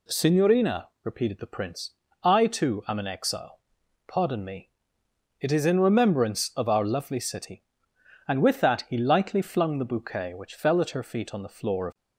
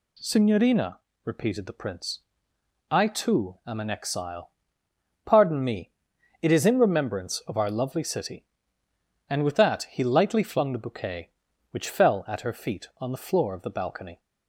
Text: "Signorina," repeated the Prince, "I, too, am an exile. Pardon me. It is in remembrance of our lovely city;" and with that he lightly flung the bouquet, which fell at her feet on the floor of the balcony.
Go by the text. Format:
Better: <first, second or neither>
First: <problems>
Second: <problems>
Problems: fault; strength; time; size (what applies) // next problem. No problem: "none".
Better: second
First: stops before "the balcony"; at 11.9 s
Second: none